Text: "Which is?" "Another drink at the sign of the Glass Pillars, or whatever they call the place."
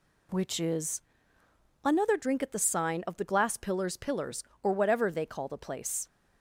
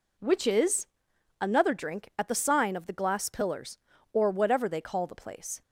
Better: second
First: says "Pillars" twice; at 3.9 s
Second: none

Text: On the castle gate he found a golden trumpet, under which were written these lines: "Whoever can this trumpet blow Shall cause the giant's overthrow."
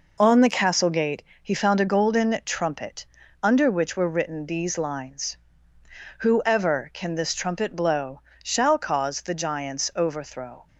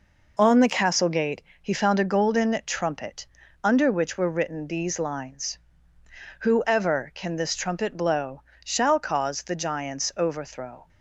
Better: neither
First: pauses between "gate" and "he"; slight; at 1.2 s; 0.22 s long // pauses between "blow" and "Shall"; slight; at 8.2 s; 0.20 s long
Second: pauses between "gate" and "he"; slight; at 1.4 s; 0.22 s long // pauses between "blow" and "Shall"; slight; at 8.4 s; 0.20 s long

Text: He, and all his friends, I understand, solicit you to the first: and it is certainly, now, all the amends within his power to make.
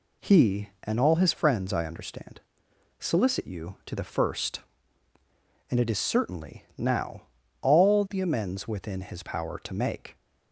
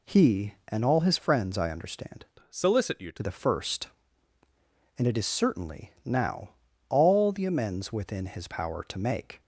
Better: first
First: none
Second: changes voice from "solicit" to "to"; from 2.4 to 3.2 s; 0.8 s long

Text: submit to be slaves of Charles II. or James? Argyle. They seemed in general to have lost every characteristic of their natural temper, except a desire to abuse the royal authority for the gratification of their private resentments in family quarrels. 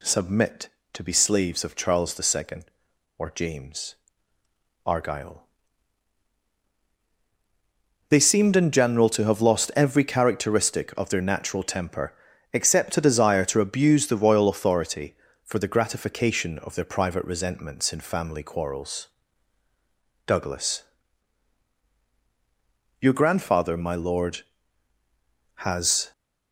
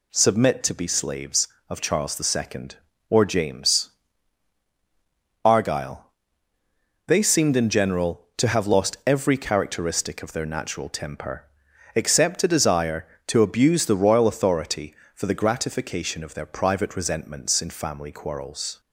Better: second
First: goes on to say "Douglas Your grandfather my lord has"; strong; from 20.2 s on; 5.8 s long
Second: none

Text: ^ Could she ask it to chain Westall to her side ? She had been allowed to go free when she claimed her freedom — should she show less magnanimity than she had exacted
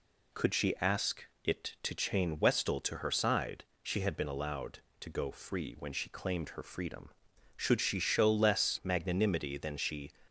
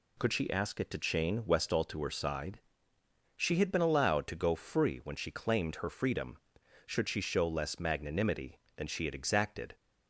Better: second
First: pauses between "ask" and "it"; slight; at 1.2 s; 0.18 s long // stops before "had exacted"; at 10.2 s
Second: none

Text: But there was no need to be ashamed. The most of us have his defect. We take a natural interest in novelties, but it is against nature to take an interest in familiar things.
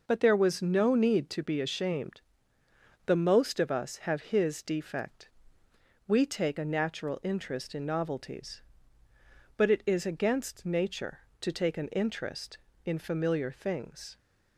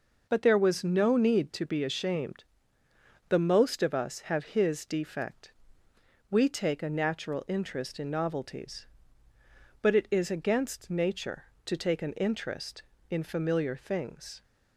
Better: neither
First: none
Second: none

